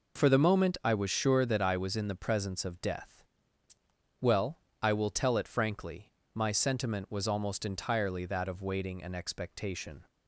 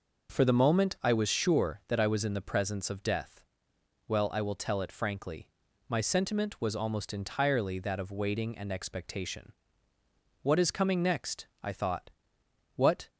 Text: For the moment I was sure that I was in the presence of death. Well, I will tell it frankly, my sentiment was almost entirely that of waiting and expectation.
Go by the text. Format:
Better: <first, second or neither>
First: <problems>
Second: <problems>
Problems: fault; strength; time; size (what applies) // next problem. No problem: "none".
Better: first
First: none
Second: goes on to say "What is coming next I thought What"; strong; from 10.4 s on; 2.6 s long